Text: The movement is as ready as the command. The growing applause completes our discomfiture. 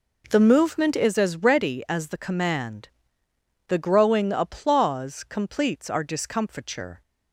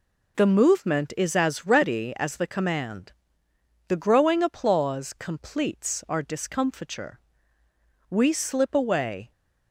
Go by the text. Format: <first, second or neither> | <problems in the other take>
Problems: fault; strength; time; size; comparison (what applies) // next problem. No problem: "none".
first | goes on to say "We slip away"; noticeable; from 8.0 s on; 1.2 s long